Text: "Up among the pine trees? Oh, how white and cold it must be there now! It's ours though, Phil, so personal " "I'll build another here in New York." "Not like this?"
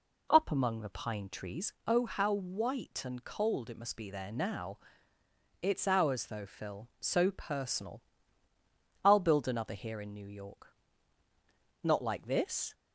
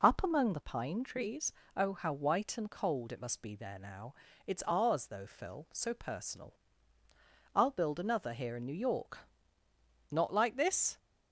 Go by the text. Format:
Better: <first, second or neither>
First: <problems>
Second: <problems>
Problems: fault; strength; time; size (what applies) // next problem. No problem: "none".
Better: neither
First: none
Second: none